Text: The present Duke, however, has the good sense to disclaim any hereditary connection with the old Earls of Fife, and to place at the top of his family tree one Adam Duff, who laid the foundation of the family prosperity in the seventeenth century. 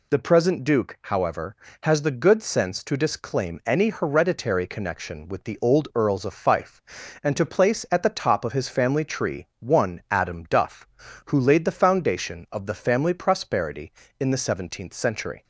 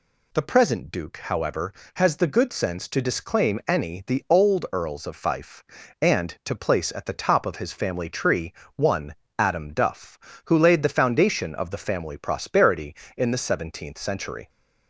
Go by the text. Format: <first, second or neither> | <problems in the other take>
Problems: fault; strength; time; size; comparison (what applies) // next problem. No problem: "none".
first | skips "hereditary connection with"; at 4.0 s // pauses between "tree" and "one"; slight; at 8.5 s; 0.24 s long // pauses between "one" and "Adam"; slight; at 9.1 s; 0.20 s long